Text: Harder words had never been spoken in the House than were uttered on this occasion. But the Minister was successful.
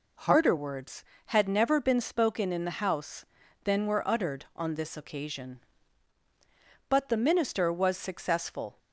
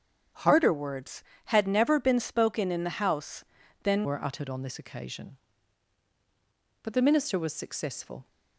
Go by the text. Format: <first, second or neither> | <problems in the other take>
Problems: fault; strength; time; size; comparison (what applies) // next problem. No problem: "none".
first | starts louder than the rest; strong; until 1.5 s; 8.5 dB // changes voice at "were"; from 4.0 s on; 4.2 s long